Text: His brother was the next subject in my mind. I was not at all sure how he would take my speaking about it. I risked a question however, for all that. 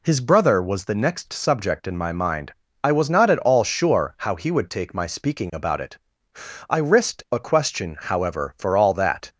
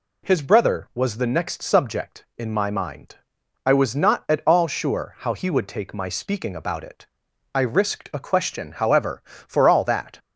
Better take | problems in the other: neither | none

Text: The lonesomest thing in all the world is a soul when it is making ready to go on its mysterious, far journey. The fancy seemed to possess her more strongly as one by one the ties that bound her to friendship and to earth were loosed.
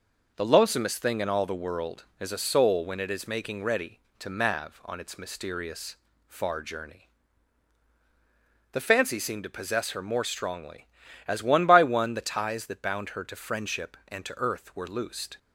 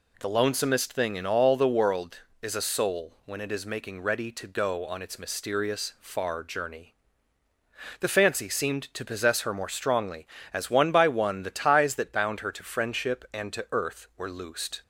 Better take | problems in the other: second | says "mav" for "go"; at 4.2 s

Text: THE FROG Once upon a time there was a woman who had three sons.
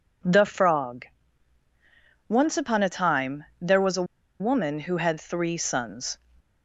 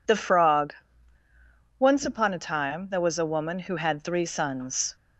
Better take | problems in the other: second | pauses between "FROG" and "Once"; at 1.0 s; 1.2 s long; also in the second // pauses between "time" and "there"; slight; at 3.4 s; 0.16 s long // pauses between "a" and "woman"; slight; at 4.0 s; 0.36 s long

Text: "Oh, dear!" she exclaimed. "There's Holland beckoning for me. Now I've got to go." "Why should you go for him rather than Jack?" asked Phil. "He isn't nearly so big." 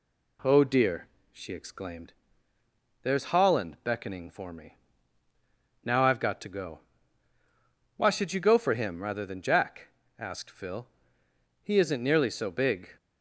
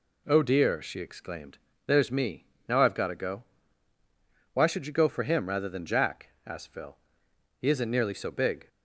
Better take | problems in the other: first | skips "Holland beckoning for"; at 2.1 s

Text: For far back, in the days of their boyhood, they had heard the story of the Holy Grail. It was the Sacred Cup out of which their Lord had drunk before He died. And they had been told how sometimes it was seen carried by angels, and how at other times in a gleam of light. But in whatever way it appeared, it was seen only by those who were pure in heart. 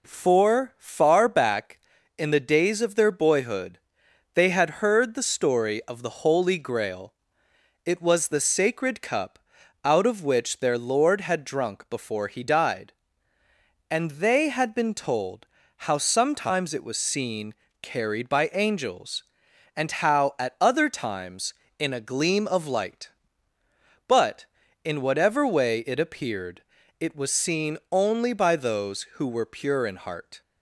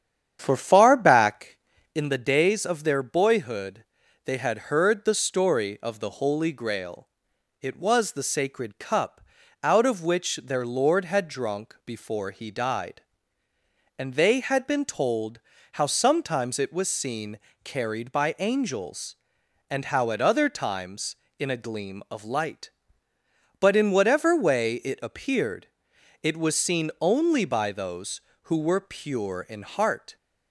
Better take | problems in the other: first | starts louder than the rest; strong; until 2.0 s; 9 dB // pauses between "Cup" and "out"; at 9.2 s; 0.42 s long; also in the first // pauses between "told" and "how"; slight; at 15.4 s; 0.32 s long; slight in the first // pauses between "seen" and "carried"; slight; at 17.3 s; 0.24 s long; slight in the first

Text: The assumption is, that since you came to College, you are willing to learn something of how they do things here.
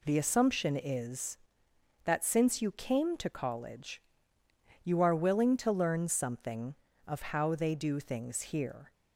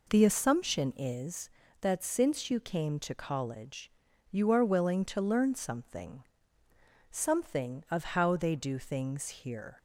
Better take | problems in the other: first | says "something" twice; at 7.1 s

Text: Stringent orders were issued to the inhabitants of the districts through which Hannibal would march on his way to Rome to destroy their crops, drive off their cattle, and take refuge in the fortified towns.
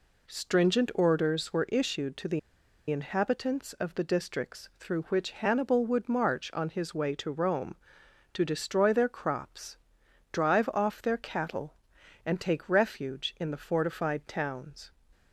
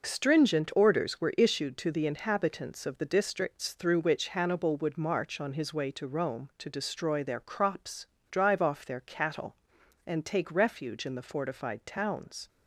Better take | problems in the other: second | pauses between "the" and "inhabitants"; noticeable; at 2.3 s; 0.50 s long

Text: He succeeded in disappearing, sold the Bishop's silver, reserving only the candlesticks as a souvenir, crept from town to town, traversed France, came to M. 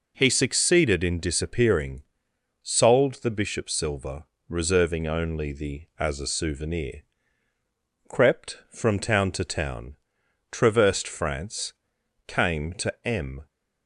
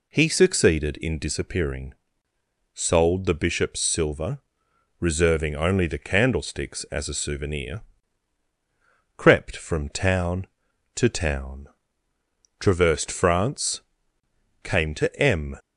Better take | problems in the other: second | skips "candlesticks"; at 5.9 s

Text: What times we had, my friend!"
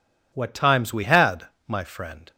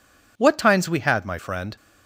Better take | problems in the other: neither | none

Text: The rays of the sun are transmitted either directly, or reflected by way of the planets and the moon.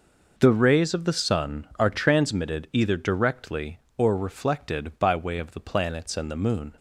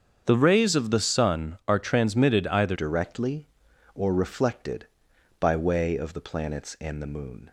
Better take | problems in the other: first | starts louder than the rest; strong; until 1.2 s; 7.5 dB // changes voice at "directly"; from 2.7 s on; 4.8 s long

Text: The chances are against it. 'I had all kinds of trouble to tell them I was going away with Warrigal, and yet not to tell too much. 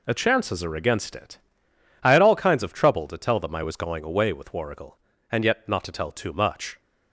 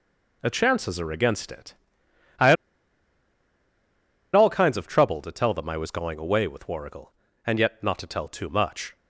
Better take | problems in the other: first | pauses between "had" and "all"; strong; at 2.5 s; 1.8 s long

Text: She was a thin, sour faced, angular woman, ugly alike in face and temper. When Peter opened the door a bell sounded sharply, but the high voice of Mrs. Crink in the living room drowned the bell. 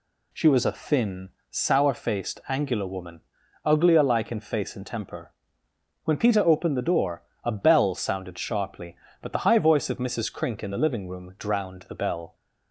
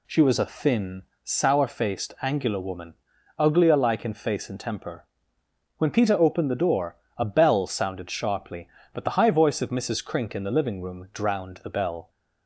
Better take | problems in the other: neither | pauses between "door" and "a"; slight; the same in both

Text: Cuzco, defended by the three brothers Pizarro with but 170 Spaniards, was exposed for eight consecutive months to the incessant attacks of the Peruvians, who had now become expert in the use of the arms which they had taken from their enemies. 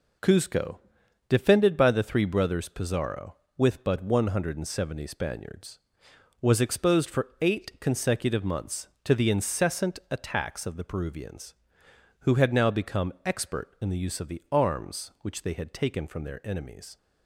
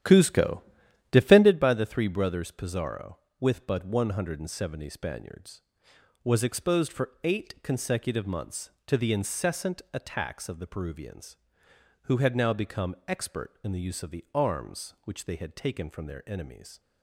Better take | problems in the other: first | starts louder than the rest; strong; until 1.6 s; 11 dB

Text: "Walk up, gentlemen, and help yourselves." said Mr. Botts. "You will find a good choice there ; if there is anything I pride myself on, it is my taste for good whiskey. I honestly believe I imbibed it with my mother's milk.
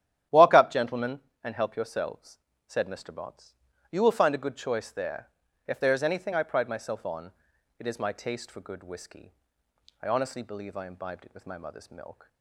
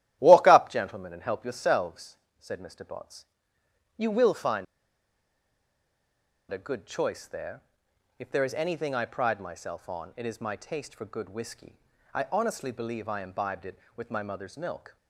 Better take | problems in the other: first | starts louder than the rest; strong; until 1.2 s; 13 dB; strong in the first // pauses between "find" and "a"; strong; at 4.6 s; 1.8 s long

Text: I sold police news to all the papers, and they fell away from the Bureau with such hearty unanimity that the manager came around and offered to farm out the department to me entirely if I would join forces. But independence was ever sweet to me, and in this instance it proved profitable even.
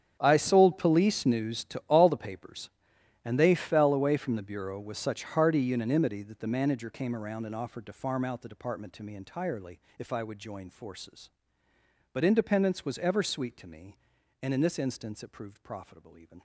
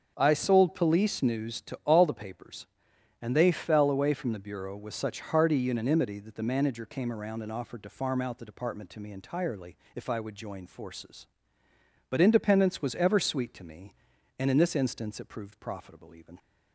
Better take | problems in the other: second | gets quieter; strong; throughout; 17 dB // starts louder than the rest; strong; until 1.2 s; 9 dB; also in the second // pauses between "entirely" and "if"; slight; at 9.7 s; 0.20 s long; slight in the second

